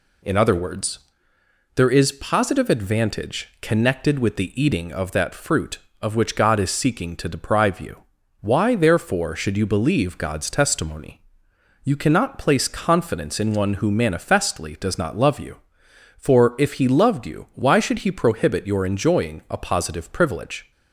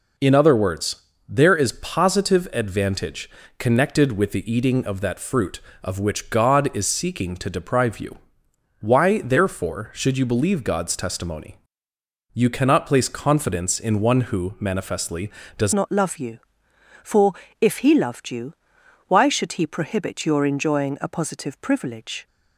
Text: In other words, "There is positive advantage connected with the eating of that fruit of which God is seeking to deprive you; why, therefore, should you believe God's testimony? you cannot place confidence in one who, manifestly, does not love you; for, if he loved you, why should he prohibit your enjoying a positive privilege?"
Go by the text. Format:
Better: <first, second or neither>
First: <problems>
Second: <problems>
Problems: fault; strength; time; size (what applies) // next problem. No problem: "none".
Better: first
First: none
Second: pauses between "advantage" and "connected"; slight; at 3.2 s; 0.30 s long // changes voice at "not"; from 15.7 s on; 6.5 s long